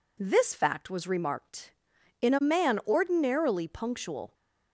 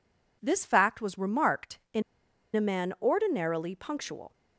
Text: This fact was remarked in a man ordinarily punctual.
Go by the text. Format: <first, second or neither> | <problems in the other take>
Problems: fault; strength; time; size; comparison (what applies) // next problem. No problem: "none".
first | pauses between "in" and "a"; noticeable; at 2.0 s; 0.54 s long